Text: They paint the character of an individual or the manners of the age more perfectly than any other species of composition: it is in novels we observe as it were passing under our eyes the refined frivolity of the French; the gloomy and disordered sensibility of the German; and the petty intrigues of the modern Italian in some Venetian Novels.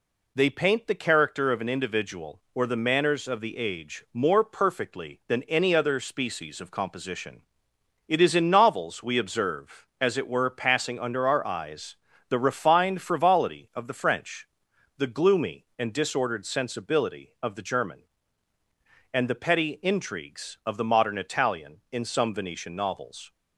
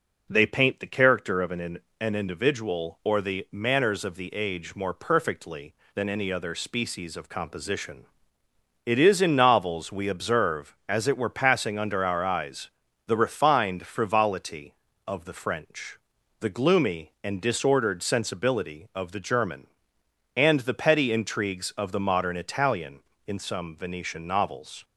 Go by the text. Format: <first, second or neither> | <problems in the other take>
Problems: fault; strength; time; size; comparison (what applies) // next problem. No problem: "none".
first | says "an" twice; at 1.9 s // pauses between "eyes" and "the"; at 12.6 s; 0.38 s long; slight in the first